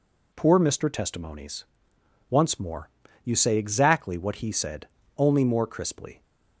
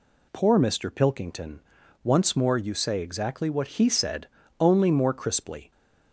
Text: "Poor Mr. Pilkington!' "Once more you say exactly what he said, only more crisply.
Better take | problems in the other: second | says "Testimonies" for "Pilkington"; at 0.8 s // pauses between "more" and "you"; slight; at 2.8 s; 0.34 s long

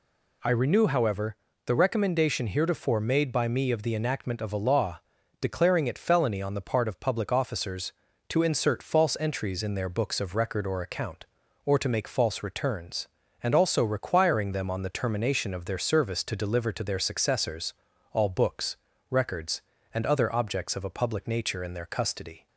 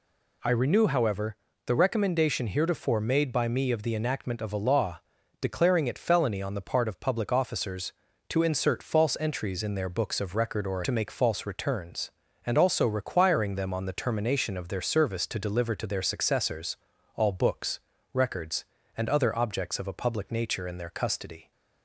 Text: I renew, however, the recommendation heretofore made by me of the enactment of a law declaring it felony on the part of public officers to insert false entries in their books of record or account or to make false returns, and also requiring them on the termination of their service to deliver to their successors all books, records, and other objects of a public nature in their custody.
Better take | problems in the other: first | pauses between "law" and "declaring"; at 4.9 s; 0.42 s long; also in the first // skips "account or"; at 10.8 s // pauses between "successors" and "all"; at 16.7 s; 0.38 s long; also in the first

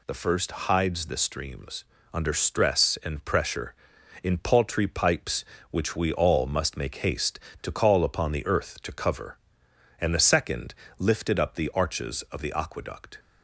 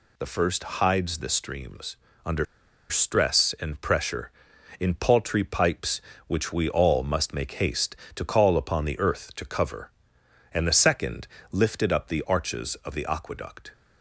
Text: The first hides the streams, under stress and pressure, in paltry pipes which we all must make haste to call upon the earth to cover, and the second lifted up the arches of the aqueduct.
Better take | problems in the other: first | pauses between "first" and "hides"; slight; at 0.6 s; 0.16 s long; slight in the first // pauses between "under" and "stress"; at 2.4 s; 0.44 s long // pauses between "second" and "lifted"; slight; at 11.2 s; 0.22 s long; slight in the first

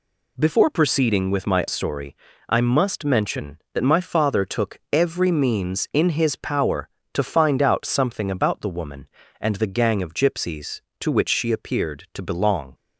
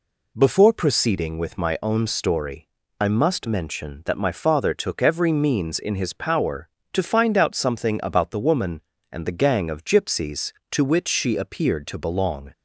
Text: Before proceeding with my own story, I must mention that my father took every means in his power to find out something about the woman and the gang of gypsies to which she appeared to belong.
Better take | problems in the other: second | skips "own"; at 1.6 s

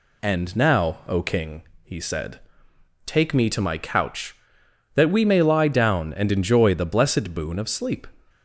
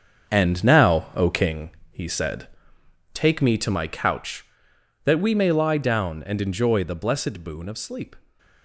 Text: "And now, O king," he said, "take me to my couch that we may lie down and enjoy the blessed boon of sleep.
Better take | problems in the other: first | gets quieter; strong; throughout; 8 dB

